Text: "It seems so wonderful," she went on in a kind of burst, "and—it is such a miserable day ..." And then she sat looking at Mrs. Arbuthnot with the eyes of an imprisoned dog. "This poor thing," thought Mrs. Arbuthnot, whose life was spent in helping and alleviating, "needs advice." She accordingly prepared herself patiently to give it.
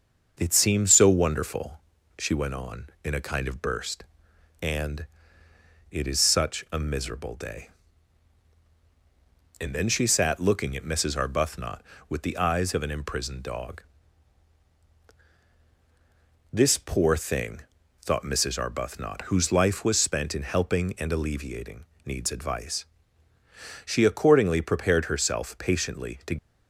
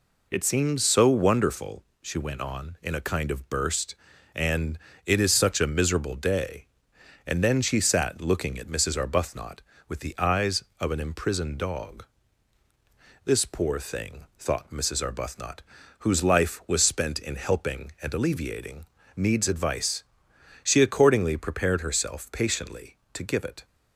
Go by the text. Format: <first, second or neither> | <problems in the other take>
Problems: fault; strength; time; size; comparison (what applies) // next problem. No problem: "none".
second | starts louder than the rest; strong; until 1.3 s; 7 dB // stops before "give it"; at 26.3 s